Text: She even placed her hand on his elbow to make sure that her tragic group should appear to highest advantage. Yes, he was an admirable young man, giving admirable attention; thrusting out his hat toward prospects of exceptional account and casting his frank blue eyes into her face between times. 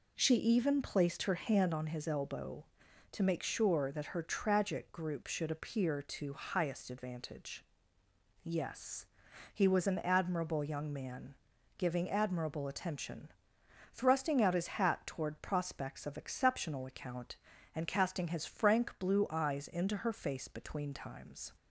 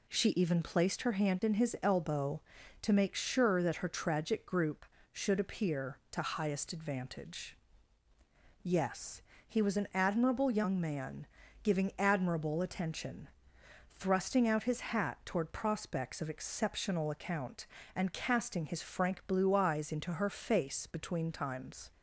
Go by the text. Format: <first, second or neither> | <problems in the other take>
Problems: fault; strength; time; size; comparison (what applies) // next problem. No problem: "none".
first | says "in" for "on"; at 1.4 s